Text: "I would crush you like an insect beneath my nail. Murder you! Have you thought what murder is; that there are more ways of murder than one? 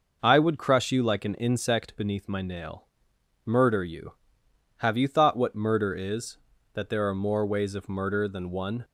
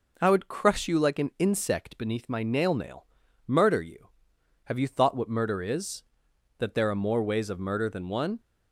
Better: first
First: none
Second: says "nail" twice; at 2.7 s

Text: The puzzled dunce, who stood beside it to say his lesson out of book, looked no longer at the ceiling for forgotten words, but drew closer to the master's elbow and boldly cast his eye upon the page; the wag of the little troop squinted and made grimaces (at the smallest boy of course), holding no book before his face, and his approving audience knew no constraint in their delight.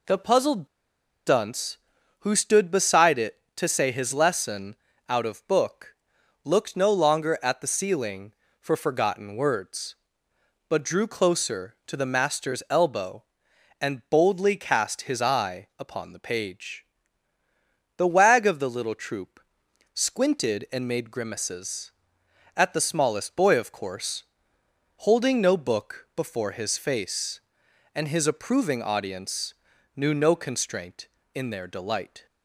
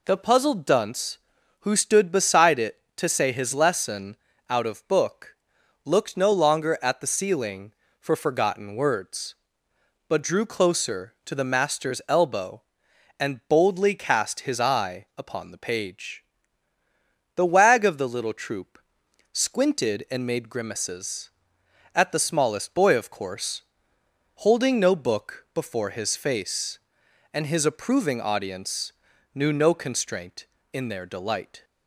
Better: second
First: pauses between "puzzled" and "dunce"; noticeable; at 0.6 s; 0.59 s long // pauses between "lesson" and "out"; slight; at 4.7 s; 0.32 s long // pauses between "troop" and "squinted"; noticeable; at 19.4 s; 0.52 s long // pauses between "audience" and "knew"; at 29.5 s; 0.42 s long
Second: pauses between "lesson" and "out"; slight; at 4.1 s; 0.32 s long // pauses between "troop" and "squinted"; noticeable; at 18.7 s; 0.52 s long // pauses between "audience" and "knew"; at 28.9 s; 0.42 s long

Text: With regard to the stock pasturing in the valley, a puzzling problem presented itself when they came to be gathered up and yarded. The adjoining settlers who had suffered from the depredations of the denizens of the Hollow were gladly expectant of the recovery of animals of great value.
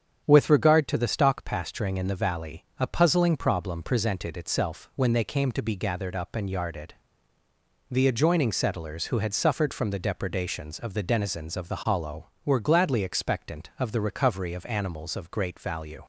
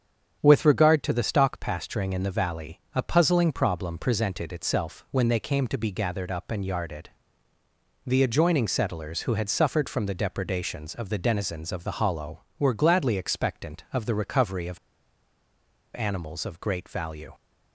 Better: first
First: starts louder than the rest; strong; until 1.2 s; 8 dB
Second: starts louder than the rest; strong; until 1.4 s; 8 dB // pauses between "of" and "animals"; at 14.7 s; 1.1 s long

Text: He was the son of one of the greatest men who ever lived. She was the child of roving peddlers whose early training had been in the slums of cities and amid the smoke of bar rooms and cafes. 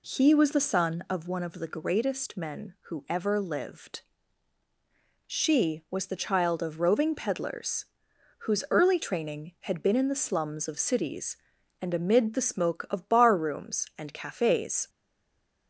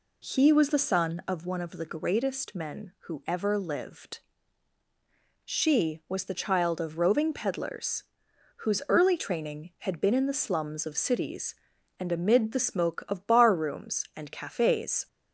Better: second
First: pauses between "peddlers" and "whose"; noticeable; at 7.8 s; 0.54 s long // stays silent after the last word; slight; from 14.8 s on; 0.8 s long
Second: pauses between "peddlers" and "whose"; noticeable; at 8.0 s; 0.54 s long

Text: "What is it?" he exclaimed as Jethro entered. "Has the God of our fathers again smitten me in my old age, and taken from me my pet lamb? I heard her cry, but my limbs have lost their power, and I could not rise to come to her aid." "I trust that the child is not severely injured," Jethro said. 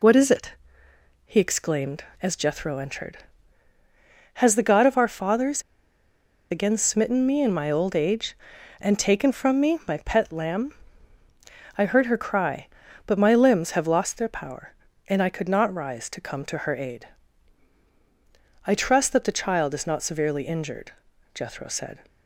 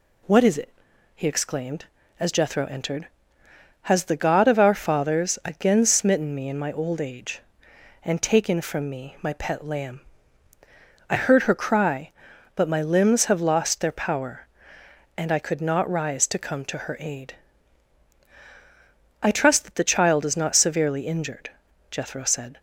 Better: second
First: pauses between "fathers" and "again"; noticeable; at 5.6 s; 0.88 s long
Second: none

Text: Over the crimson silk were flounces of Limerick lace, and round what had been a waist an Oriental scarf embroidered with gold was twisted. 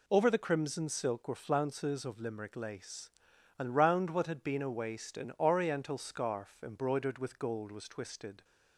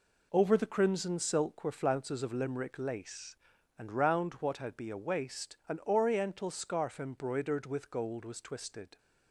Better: first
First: none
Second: says "be" for "been"; at 4.7 s

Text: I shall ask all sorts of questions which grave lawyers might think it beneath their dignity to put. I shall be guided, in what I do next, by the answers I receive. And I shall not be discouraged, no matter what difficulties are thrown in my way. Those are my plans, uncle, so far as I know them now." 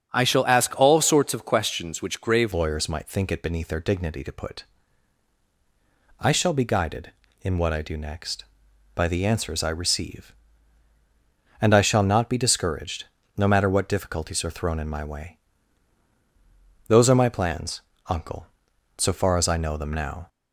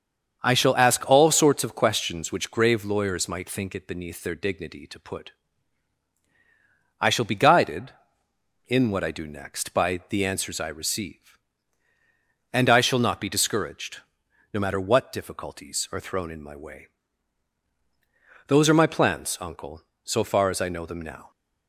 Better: second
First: starts louder than the rest; strong; until 1.1 s; 7.5 dB // changes voice at "lawyers"; from 2.5 s on; 17.7 s long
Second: starts louder than the rest; until 1.4 s; 7 dB

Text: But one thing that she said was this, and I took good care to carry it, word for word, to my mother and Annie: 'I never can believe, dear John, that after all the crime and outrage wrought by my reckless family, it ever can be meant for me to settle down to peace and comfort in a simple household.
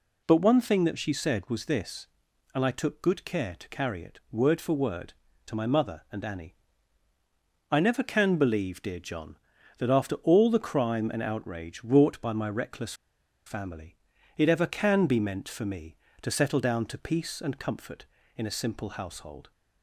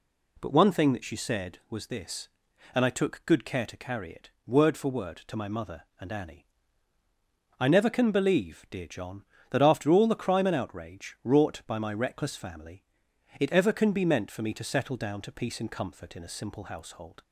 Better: second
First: pauses between "reckless" and "family"; noticeable; at 12.9 s; 0.53 s long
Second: none

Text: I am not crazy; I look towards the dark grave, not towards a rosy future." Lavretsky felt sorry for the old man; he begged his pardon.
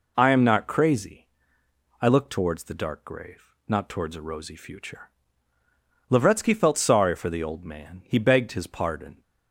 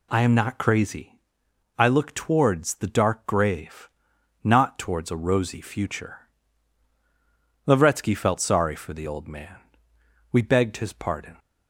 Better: first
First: none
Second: says "we" for "he"; at 10.3 s

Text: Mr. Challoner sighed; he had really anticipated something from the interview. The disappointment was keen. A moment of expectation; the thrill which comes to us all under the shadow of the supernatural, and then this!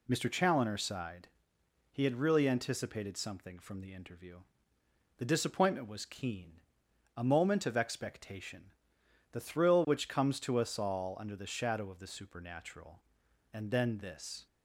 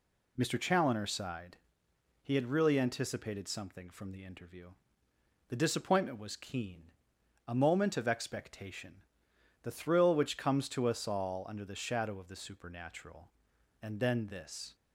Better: neither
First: none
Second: none

